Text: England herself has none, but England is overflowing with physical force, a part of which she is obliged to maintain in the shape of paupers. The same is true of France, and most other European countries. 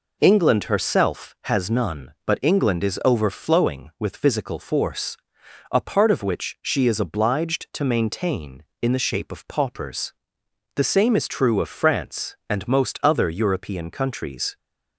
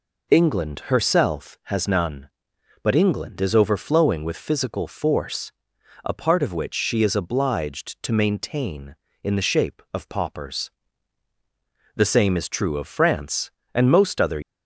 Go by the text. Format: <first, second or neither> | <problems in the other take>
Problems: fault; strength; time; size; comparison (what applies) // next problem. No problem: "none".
first | stops before "European countries"; at 14.4 s